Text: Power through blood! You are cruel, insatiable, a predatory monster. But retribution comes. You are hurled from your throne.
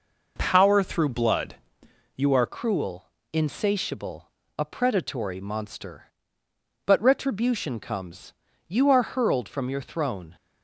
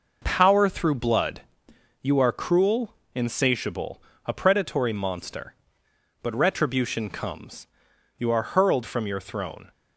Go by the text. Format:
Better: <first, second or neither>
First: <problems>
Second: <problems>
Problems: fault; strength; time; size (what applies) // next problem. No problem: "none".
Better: second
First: changes voice at "cruel"; from 2.4 s on; 7.9 s long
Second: none